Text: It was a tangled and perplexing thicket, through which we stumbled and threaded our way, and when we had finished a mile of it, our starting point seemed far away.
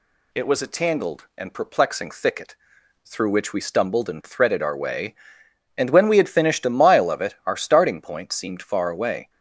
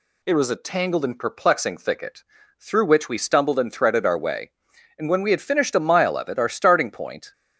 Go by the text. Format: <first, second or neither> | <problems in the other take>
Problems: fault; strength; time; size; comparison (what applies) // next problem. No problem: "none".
first | stops before "seemed far away"; at 7.3 s